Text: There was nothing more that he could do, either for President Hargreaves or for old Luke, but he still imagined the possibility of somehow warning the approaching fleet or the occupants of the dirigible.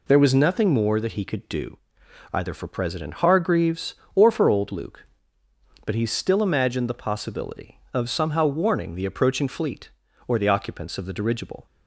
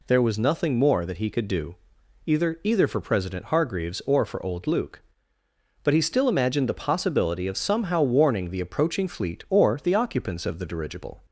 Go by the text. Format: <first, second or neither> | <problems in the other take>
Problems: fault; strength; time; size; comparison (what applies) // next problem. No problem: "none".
first | says "either" twice; at 2.6 s